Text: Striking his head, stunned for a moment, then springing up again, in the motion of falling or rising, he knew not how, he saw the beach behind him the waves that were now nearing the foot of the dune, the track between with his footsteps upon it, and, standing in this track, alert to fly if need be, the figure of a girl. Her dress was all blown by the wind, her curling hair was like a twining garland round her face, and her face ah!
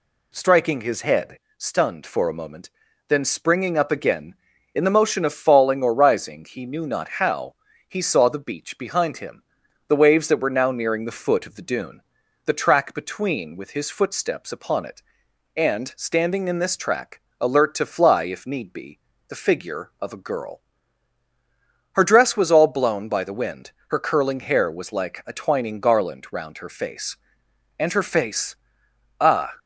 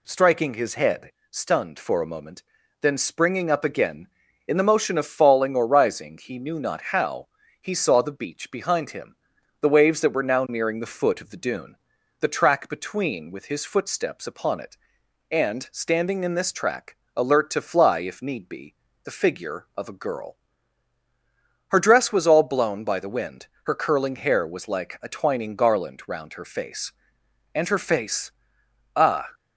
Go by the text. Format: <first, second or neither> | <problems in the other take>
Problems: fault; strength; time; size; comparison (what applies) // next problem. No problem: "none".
neither | pauses between "him" and "the"; noticeable; the same in both // pauses between "face" and "ah"; noticeable; the same in both